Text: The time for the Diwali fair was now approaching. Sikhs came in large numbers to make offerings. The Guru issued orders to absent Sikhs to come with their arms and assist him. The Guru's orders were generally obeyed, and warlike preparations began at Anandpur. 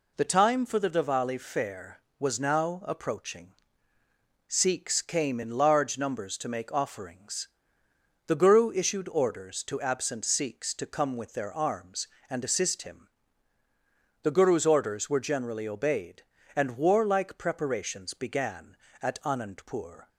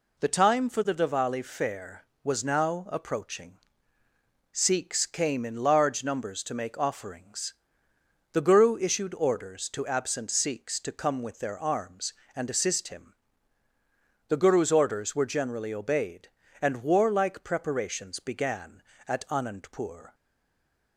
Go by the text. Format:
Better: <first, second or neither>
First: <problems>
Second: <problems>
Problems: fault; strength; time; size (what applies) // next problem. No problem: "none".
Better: first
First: none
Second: stays silent after the last word; slight; from 20.1 s on; 0.8 s long